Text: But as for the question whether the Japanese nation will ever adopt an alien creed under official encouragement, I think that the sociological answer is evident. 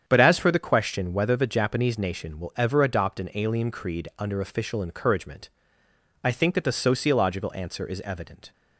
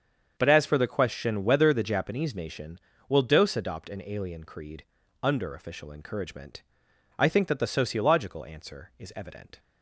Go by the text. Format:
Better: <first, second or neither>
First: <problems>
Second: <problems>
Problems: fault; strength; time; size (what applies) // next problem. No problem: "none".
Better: first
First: starts louder than the rest; strong; until 1.0 s; 8.5 dB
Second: starts louder than the rest; until 1.3 s; 7 dB // says "dose" for "ever"; at 3.2 s // pauses between "creed" and "under"; at 4.8 s; 0.40 s long